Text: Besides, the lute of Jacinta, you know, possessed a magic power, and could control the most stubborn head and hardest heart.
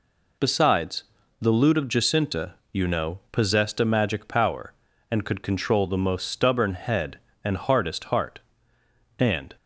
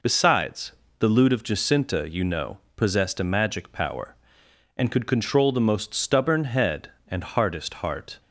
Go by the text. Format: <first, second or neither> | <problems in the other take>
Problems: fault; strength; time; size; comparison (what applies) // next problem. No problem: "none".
second | goes on to say "And"; slight; from 9.1 s on; 0.38 s long